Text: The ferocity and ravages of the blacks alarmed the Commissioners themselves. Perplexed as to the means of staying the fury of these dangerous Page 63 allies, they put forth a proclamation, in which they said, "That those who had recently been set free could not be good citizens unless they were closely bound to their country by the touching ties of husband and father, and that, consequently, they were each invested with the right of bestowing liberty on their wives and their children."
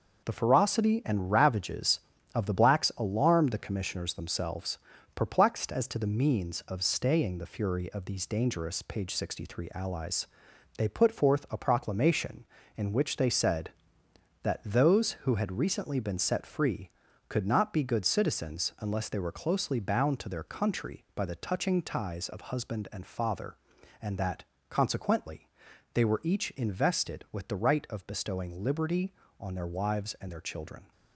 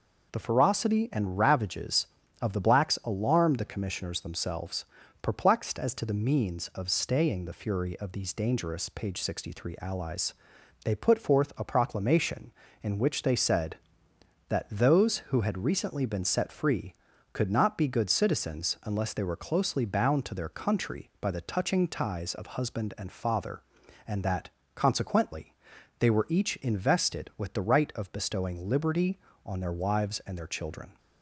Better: second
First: gets quieter; throughout; 6.5 dB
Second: none

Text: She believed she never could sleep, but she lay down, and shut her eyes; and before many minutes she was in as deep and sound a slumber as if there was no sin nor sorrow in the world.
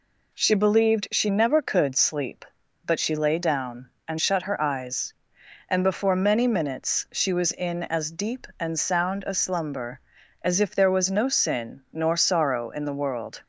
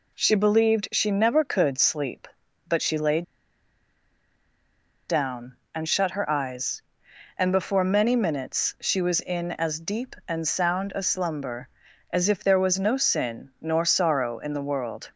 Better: first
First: none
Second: pauses between "lay" and "down"; strong; at 3.2 s; 1.8 s long

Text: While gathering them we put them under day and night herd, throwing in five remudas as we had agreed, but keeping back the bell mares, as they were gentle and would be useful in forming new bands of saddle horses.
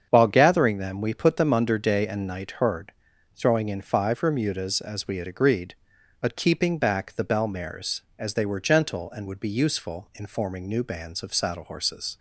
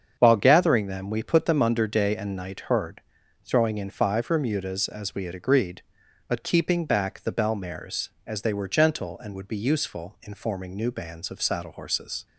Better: neither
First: starts louder than the rest; strong; until 1.1 s; 7.5 dB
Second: starts louder than the rest; strong; until 1.2 s; 7.5 dB

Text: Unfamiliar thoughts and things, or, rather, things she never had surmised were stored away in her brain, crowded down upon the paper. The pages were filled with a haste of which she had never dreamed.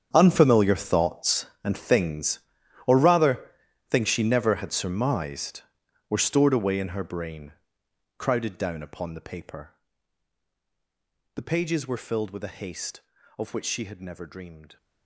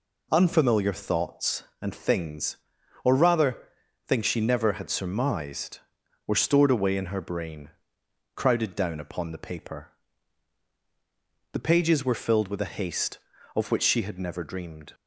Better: second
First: gets quieter; strong; throughout; 15.5 dB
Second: none

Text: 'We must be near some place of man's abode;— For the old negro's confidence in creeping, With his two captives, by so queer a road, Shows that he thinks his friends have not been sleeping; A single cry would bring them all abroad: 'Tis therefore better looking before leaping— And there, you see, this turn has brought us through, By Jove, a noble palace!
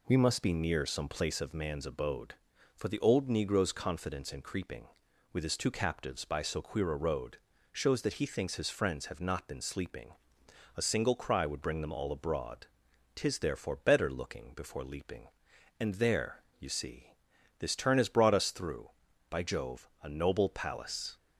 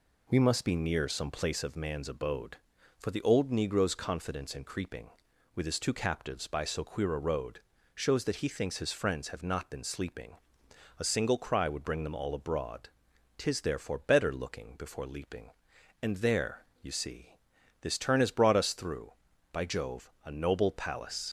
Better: first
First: none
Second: leaves "palace" unfinished; at 21.2 s; 70 ms

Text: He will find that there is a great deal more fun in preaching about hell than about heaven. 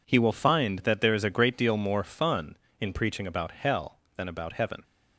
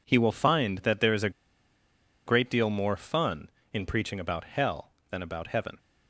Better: first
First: none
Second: pauses between "a" and "great"; noticeable; at 1.2 s; 0.96 s long

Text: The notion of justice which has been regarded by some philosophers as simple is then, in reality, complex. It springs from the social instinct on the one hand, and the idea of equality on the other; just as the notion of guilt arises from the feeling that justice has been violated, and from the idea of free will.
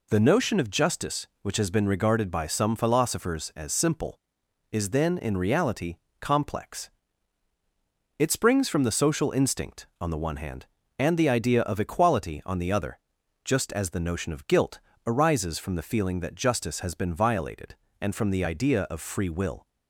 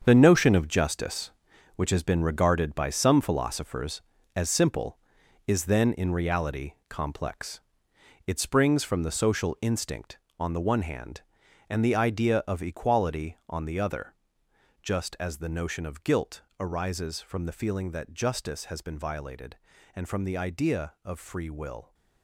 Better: first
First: pauses between "guilt" and "arises"; slight; at 14.7 s; 0.28 s long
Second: gets quieter; strong; throughout; 10.5 dB // pauses between "guilt" and "arises"; slight; at 16.4 s; 0.18 s long

